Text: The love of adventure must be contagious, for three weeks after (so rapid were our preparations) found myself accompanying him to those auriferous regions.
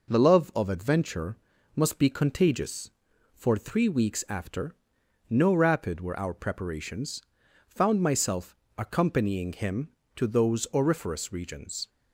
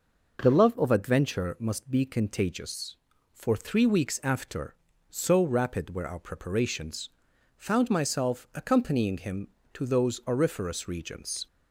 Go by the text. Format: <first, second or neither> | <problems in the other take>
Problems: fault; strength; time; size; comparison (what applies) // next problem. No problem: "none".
second | pauses between "adventure" and "must"; at 1.3 s; 0.38 s long // says "no" for "so"; at 5.2 s // pauses between "myself" and "accompanying"; slight; at 8.5 s; 0.20 s long